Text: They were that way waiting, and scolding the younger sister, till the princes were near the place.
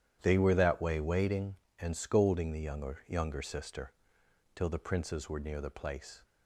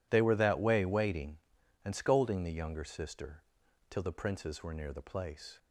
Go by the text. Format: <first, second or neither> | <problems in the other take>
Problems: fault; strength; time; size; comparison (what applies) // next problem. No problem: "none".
second | starts louder than the rest; strong; until 1.2 s; 10.5 dB // says "younger" twice; at 3.0 s